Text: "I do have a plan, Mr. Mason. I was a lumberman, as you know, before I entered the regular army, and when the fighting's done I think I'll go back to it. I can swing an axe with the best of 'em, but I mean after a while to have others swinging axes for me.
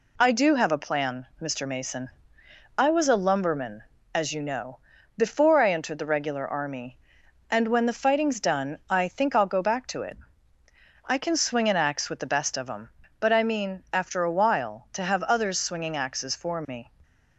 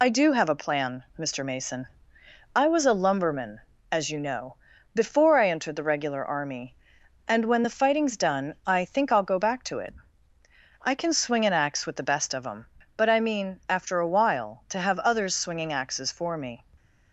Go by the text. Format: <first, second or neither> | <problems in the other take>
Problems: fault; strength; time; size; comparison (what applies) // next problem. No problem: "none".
first | loses the start of "I"; at 0.0 s; 80 ms